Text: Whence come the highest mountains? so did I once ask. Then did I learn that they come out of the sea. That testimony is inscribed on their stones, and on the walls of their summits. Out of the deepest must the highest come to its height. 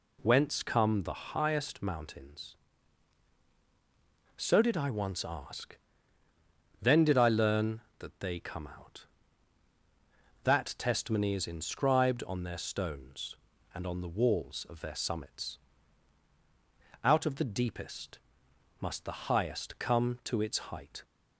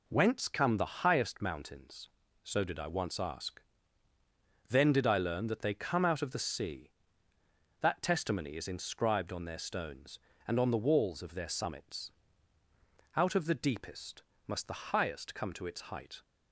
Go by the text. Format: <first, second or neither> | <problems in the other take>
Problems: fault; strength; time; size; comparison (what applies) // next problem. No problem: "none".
second | skips "of the sea"; at 9.7 s // pauses between "deepest" and "must"; noticeable; at 18.1 s; 0.62 s long; slight in the second